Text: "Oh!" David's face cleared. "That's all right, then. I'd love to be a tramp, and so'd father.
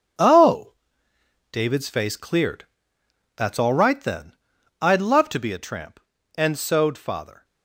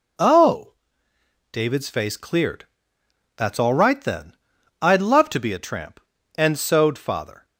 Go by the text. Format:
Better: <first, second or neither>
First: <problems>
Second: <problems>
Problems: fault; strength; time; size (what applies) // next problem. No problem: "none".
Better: second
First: gets quieter; strong; throughout; 9.5 dB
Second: none